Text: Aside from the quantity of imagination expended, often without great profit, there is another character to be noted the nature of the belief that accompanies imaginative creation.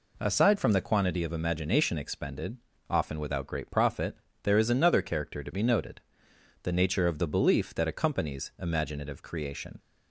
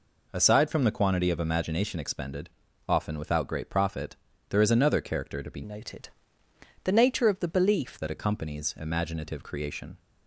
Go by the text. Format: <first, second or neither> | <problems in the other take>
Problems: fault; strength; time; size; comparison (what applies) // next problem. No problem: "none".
first | changes voice from "noted" to "belief"; from 5.6 to 7.9 s; 2.3 s long // pauses between "noted" and "the"; noticeable; at 6.0 s; 0.76 s long; noticeable in the first